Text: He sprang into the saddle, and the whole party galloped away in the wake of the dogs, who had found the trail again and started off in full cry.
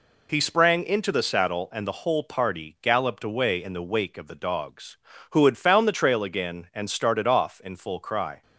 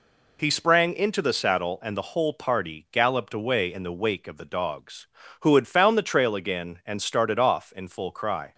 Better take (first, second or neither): neither